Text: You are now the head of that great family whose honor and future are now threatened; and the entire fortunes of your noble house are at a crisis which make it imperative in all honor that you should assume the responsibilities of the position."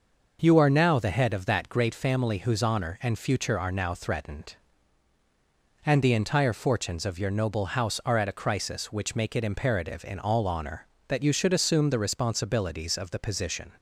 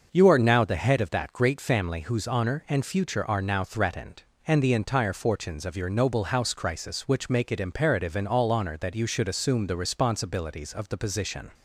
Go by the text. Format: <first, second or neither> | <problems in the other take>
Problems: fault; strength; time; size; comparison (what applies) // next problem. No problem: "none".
first | skips "are at a"; at 6.5 s